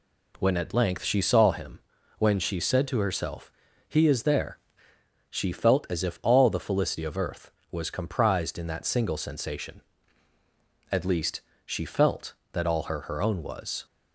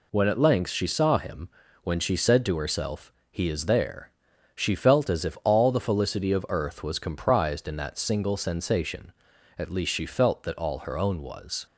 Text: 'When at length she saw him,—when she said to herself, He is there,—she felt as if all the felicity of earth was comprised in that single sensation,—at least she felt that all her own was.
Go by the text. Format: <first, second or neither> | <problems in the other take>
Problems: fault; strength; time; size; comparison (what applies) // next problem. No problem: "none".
second | pauses between "least" and "she"; slight; at 11.4 s; 0.24 s long // says "her" twice; at 13.0 s